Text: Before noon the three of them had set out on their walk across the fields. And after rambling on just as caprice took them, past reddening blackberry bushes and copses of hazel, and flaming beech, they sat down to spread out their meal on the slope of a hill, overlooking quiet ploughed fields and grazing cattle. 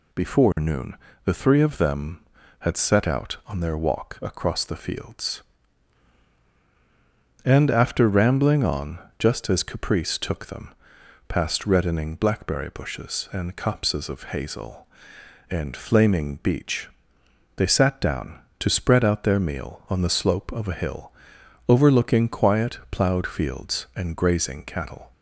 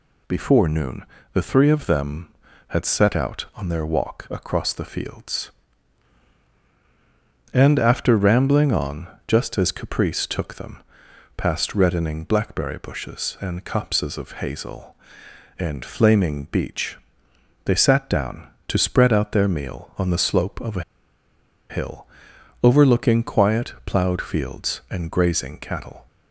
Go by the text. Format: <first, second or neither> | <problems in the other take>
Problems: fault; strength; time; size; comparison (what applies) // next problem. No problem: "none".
first | pauses between "noon" and "the"; slight; at 1.0 s; 0.28 s long; slight in the first // pauses between "on" and "just"; slight; at 9.0 s; 0.20 s long; slight in the first // pauses between "a" and "hill"; noticeable; at 20.8 s; 0.87 s long